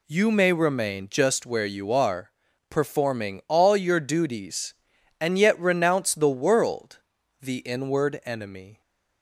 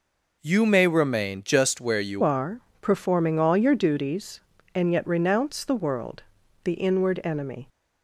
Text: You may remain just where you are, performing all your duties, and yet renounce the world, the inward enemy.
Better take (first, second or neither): first